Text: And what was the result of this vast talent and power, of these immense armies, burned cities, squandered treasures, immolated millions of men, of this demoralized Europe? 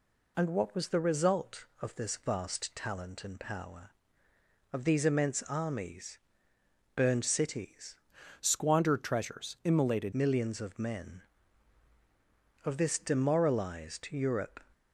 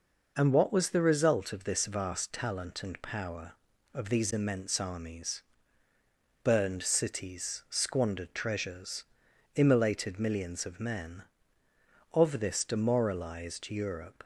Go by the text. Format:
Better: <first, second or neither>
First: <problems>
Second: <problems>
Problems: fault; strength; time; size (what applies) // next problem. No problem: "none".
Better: second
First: changes voice from "squandered" to "immolated"; from 8.3 to 10.1 s; 1.8 s long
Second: none